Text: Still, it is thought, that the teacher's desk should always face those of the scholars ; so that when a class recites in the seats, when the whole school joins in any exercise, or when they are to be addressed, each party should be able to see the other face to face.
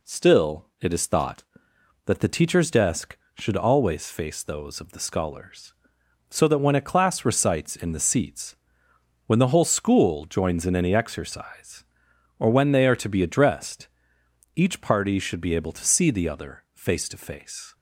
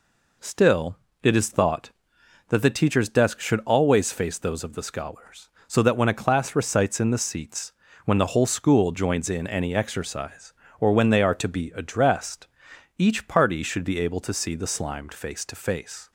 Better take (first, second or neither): first